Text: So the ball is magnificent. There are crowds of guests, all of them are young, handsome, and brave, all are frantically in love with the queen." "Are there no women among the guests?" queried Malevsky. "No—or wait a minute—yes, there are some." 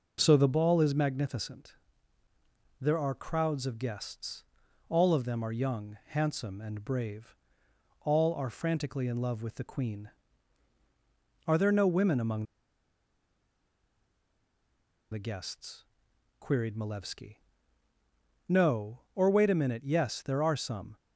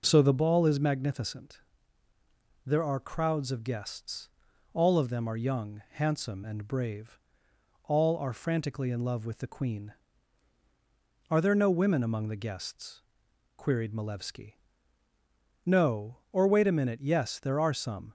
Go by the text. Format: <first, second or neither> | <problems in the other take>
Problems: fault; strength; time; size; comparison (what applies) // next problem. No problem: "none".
second | pauses between "among" and "the"; strong; at 12.4 s; 2.6 s long